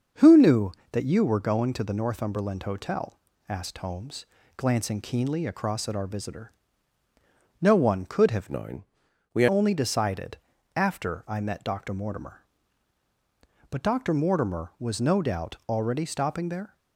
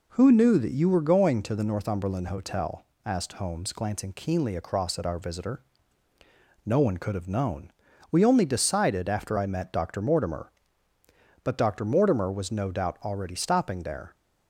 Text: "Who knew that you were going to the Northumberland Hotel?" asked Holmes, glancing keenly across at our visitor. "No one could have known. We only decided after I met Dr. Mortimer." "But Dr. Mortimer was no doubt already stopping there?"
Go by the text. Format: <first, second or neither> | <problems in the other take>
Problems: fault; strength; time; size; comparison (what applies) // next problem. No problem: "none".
second | starts louder than the rest; noticeable; until 1.3 s; 6 dB // changes voice from "known" to "We"; from 8.5 to 9.4 s; 0.9 s long // pauses between "decided" and "after"; at 10.3 s; 0.38 s long